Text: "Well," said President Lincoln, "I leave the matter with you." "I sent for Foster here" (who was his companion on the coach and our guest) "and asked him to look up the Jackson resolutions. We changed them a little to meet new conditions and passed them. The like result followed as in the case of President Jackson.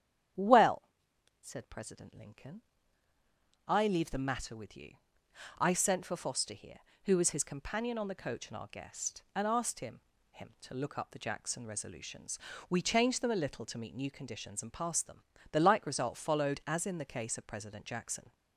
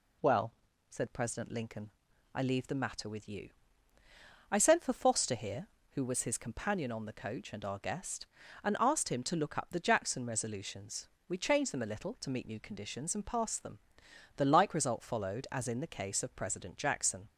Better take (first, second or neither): second